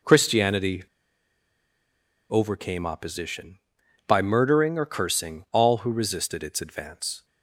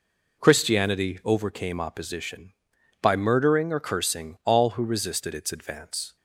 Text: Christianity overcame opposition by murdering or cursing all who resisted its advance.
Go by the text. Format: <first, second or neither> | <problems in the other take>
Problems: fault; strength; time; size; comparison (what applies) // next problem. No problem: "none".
second | pauses between "Christianity" and "overcame"; strong; at 0.8 s; 1.4 s long